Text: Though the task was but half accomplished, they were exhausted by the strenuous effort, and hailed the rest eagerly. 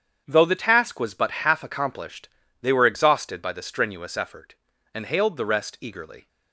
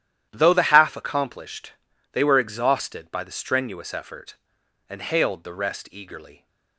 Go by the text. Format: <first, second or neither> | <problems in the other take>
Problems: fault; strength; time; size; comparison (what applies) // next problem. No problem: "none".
first | starts louder than the rest; strong; until 1.3 s; 11.5 dB; strong in the first // skips "task was but"; at 0.6 s